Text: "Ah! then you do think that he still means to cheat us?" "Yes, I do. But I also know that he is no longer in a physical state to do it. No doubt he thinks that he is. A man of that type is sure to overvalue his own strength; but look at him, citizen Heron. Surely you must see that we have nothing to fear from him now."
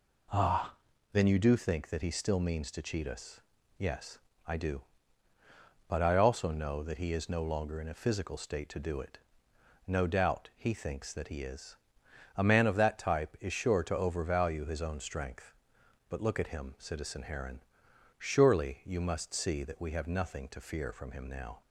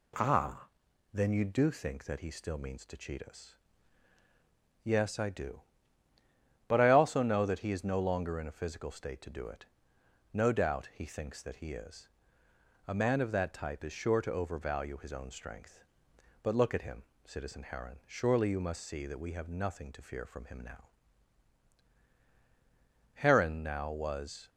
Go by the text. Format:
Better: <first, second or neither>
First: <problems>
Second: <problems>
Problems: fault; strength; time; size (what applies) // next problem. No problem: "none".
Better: first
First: none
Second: goes on to say "Heron now was"; from 23.1 s on; 1.3 s long